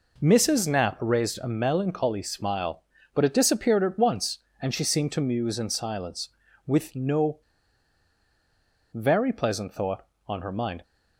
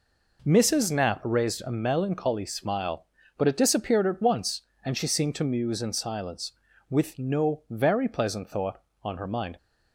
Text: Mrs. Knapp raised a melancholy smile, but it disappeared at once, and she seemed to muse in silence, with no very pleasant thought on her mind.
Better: second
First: pauses between "no" and "very"; strong; at 7.3 s; 1.5 s long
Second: none

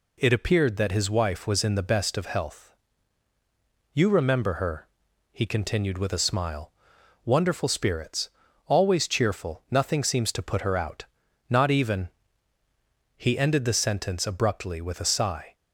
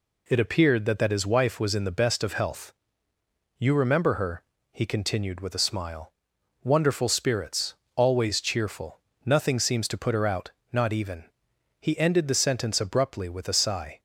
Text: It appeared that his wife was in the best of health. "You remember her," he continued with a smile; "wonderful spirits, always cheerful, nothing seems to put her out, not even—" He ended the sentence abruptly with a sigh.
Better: first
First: none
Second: says "that" twice; at 0.9 s

